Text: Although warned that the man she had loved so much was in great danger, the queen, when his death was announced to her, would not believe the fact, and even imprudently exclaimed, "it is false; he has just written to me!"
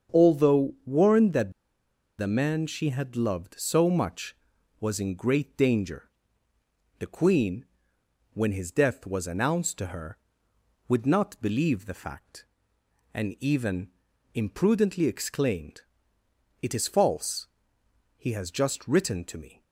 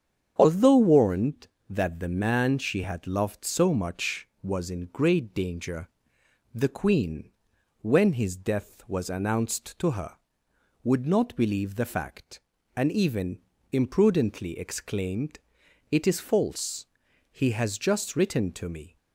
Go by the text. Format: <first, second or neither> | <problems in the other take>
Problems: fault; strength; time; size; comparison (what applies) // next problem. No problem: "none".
second | starts louder than the rest; strong; until 1.2 s; 7 dB; strong in the second // pauses between "that" and "the"; noticeable; at 1.5 s; 0.66 s long // pauses between "even" and "imprudently"; noticeable; at 13.8 s; 0.46 s long; slight in the second